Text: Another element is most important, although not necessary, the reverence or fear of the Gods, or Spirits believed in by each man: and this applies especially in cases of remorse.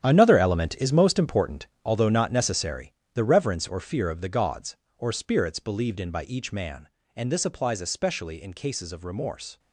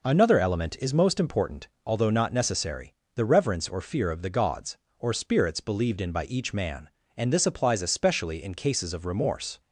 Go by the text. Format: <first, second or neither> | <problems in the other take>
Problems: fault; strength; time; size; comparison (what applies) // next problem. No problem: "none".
second | gets quieter; strong; throughout; 12 dB